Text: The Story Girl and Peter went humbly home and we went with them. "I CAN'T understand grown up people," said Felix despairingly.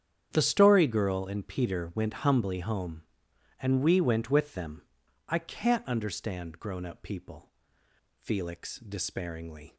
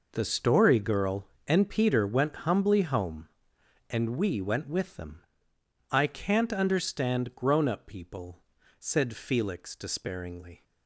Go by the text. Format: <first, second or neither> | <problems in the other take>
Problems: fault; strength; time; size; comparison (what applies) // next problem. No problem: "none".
second | starts louder than the rest; strong; until 1.3 s; 9 dB // skips "said"; at 7.8 s